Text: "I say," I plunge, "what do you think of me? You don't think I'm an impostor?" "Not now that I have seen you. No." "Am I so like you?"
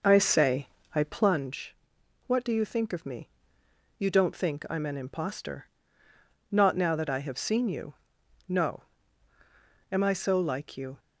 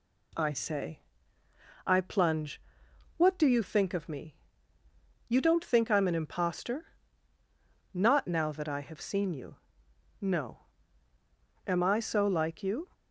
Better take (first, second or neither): second